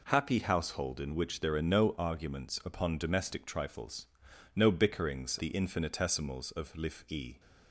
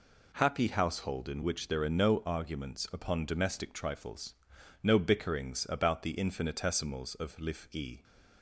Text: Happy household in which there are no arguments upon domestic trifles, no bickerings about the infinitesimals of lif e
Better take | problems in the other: second | skips "about"; at 5.3 s

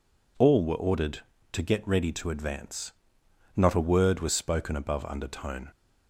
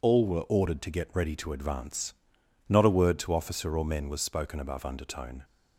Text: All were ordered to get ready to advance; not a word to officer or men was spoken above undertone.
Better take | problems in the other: second | skips "to officer or men"; at 4.1 s

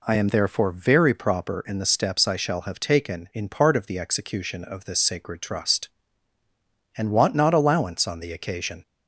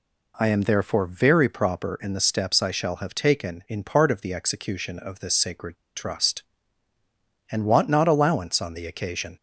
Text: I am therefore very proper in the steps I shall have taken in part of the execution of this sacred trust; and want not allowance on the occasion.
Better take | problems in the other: first | pauses between "sacred" and "trust"; slight; at 5.7 s; 0.21 s long

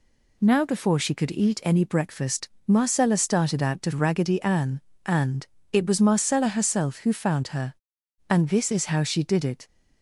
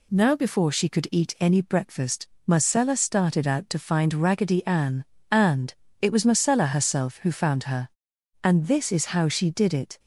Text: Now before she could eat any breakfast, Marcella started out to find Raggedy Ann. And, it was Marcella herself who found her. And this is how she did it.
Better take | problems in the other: second | skips "find"; at 3.9 s

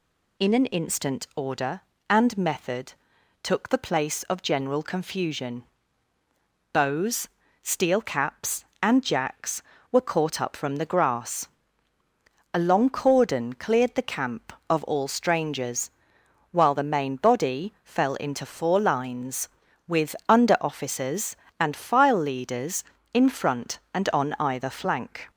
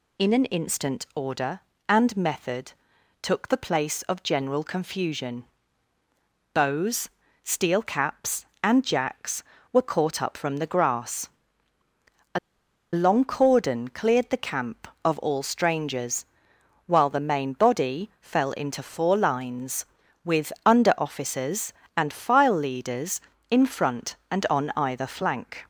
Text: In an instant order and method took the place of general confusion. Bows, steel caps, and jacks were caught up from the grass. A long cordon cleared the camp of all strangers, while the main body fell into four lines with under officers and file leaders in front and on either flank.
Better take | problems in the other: first | pauses between "method" and "took"; noticeable; at 2.7 s; 0.50 s long; noticeable in the first // pauses between "A" and "long"; noticeable; at 12.3 s; 0.54 s long

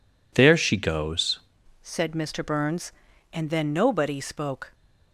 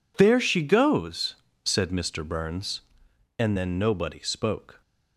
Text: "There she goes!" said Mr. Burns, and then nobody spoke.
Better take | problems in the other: second | changes voice at "said"; from 1.8 s on; 2.9 s long

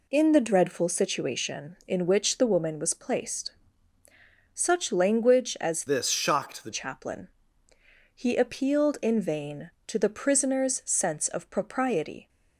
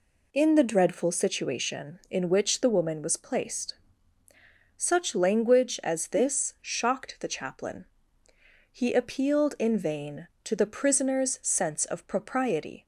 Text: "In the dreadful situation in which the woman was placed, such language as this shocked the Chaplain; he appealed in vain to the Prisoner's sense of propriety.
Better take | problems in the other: second | changes voice from "this" to "the"; from 5.8 to 6.7 s; 0.9 s long

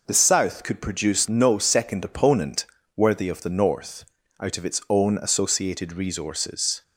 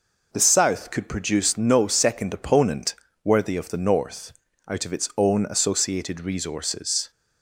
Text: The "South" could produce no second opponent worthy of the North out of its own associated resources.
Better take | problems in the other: neither | pauses between "opponent" and "worthy"; slight; the same in both // pauses between "North" and "out"; the same in both

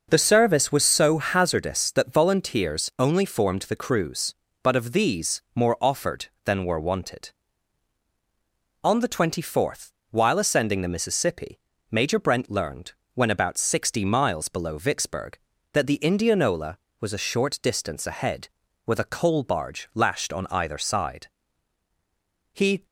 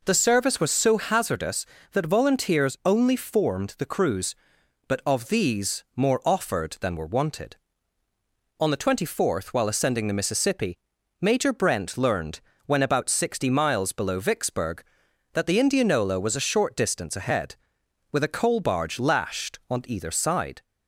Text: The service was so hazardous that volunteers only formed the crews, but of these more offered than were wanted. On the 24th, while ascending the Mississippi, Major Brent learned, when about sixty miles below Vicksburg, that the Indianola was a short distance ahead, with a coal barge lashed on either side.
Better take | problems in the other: second | goes on to say "He"; slight; from 22.5 s on; 0.34 s long

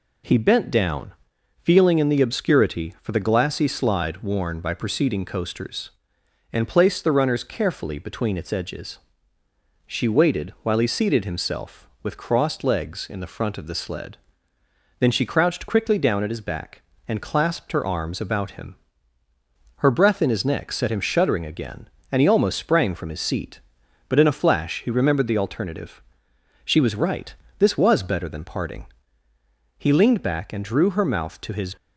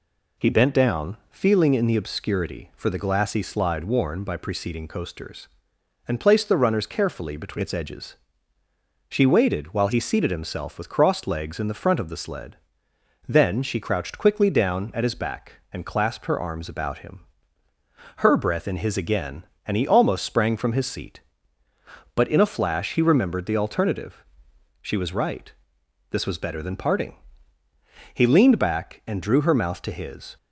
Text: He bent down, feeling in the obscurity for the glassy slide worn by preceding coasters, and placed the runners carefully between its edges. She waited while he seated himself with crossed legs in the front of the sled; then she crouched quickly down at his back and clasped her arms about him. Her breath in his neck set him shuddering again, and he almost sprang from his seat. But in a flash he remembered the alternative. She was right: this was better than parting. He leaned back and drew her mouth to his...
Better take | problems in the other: first | skips "neck set him shuddering"; at 18.9 s

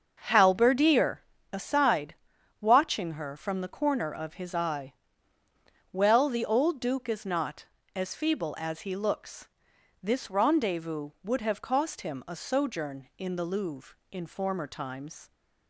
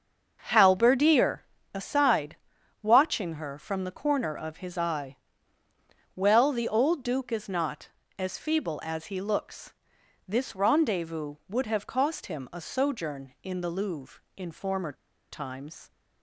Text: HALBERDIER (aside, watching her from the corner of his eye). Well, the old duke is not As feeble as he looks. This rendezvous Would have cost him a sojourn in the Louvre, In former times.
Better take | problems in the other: first | starts louder than the rest; until 1.7 s; 6.5 dB; also in the first // pauses between "former" and "times"; at 14.9 s; 0.37 s long

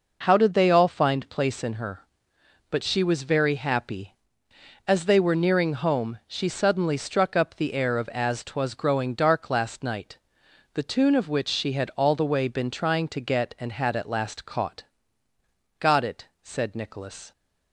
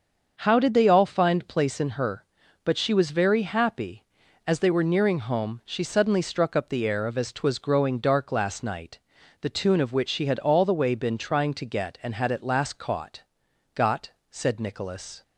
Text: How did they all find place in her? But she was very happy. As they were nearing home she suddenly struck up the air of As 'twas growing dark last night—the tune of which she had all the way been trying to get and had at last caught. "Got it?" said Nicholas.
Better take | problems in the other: first | starts louder than the rest; until 1.4 s; 6.5 dB // skips "it"; at 14.2 s

